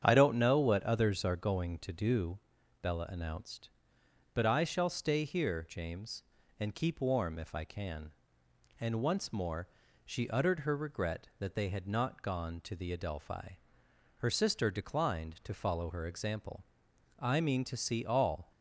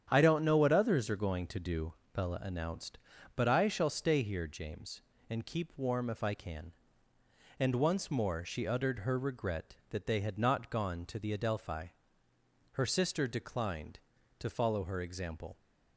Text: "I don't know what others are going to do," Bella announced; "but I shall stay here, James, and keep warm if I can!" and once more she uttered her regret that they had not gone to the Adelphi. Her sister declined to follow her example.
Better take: second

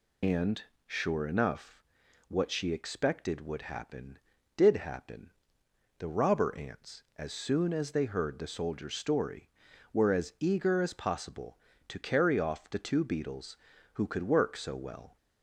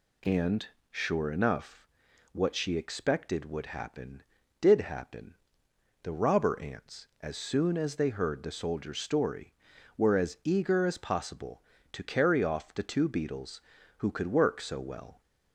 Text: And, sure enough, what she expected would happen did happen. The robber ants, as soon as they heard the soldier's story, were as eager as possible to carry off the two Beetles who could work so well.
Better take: second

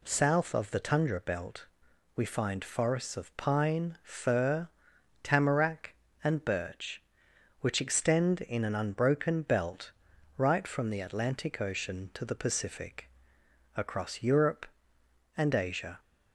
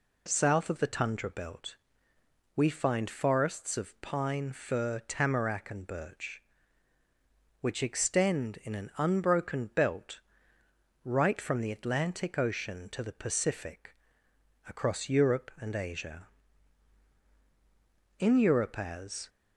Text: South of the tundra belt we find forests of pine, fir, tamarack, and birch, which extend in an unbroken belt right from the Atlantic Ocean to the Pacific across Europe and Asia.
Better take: first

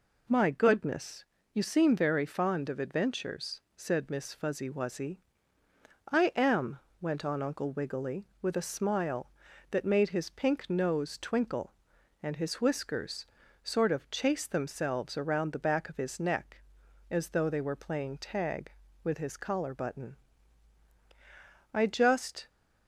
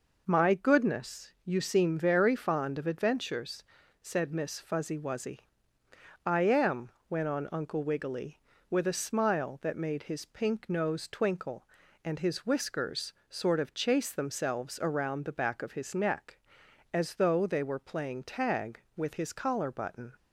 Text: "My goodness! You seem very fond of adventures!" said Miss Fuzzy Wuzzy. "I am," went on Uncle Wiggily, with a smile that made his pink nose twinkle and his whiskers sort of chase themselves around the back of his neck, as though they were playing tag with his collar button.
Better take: second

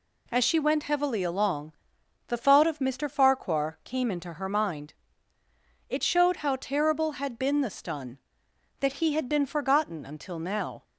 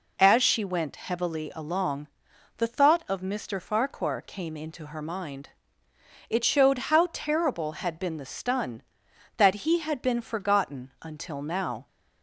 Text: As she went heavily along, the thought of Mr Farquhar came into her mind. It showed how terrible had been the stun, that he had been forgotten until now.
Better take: neither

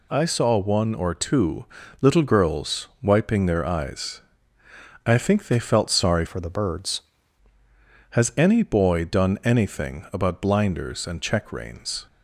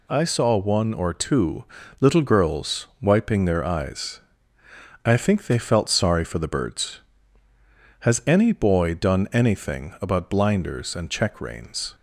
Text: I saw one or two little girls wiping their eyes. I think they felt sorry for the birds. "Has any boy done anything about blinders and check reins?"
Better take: second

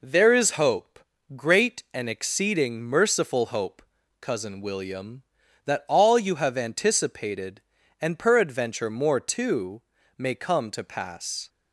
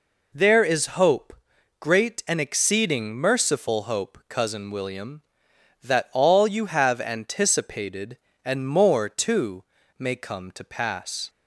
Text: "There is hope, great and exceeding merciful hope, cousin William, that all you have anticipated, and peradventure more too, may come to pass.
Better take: first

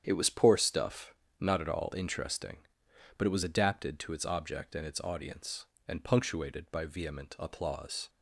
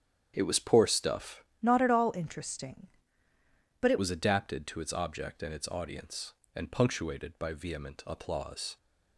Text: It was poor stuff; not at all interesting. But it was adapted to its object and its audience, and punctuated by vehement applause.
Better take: first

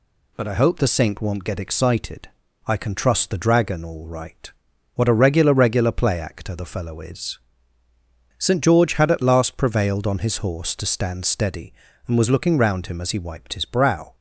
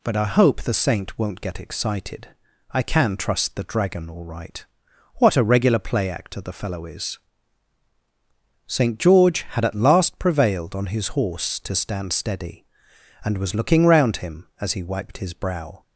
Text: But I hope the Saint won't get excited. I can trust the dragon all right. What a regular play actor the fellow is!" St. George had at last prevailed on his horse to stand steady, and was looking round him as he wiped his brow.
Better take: second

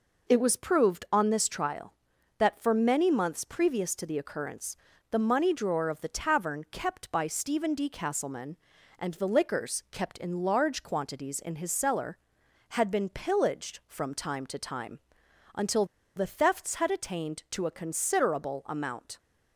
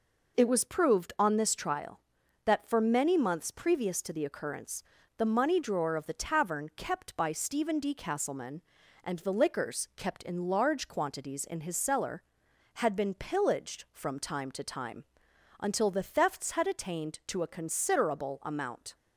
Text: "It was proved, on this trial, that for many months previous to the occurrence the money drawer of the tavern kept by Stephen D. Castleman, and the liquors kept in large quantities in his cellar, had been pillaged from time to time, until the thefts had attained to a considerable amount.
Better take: second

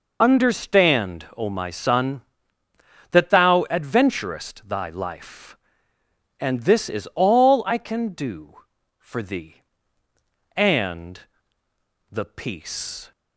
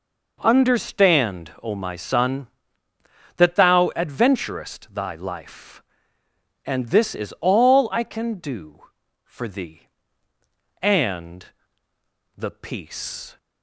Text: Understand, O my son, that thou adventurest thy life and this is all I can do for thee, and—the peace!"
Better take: second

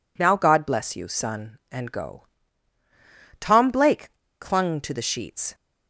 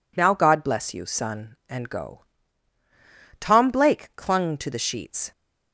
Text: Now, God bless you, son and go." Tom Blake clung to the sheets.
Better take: second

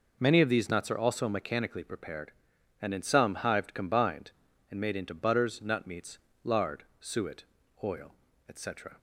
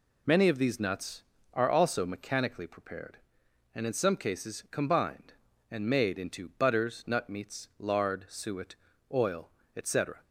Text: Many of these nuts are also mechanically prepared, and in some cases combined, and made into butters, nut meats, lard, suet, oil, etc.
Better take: second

